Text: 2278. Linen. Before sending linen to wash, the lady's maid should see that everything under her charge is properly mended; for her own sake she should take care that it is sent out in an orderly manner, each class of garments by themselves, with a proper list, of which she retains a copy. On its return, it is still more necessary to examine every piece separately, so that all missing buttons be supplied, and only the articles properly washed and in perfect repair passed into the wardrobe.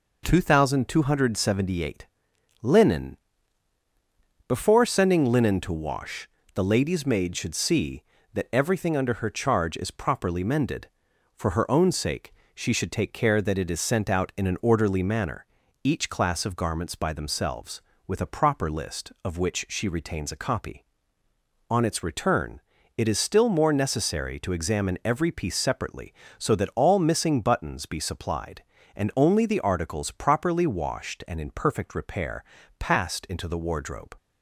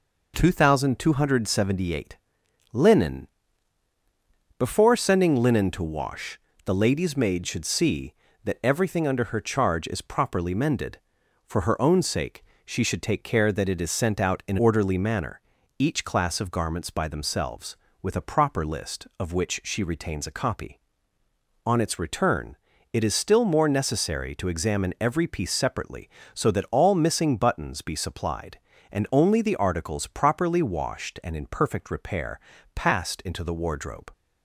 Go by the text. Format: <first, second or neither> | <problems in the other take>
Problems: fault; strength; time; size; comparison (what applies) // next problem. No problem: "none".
first | pauses between "sake" and "she"; slight; at 12.4 s; 0.22 s long; slight in the first // skips "an"; at 14.5 s // pauses between "repair" and "passed"; slight; at 32.3 s; 0.34 s long; slight in the first